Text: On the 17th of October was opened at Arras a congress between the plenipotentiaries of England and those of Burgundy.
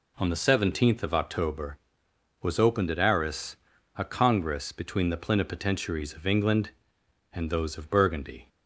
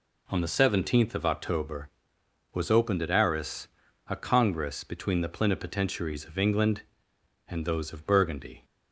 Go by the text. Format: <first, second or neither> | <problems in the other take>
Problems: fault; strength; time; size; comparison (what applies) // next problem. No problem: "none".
neither | pauses between "Arras" and "a"; the same in both